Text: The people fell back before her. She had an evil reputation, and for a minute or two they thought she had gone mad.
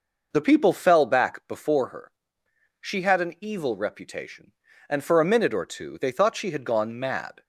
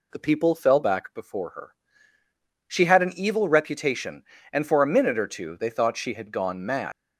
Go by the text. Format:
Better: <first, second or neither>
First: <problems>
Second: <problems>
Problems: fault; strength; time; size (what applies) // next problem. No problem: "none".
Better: first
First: none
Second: leaves "mad" unfinished; at 6.9 s; 125 ms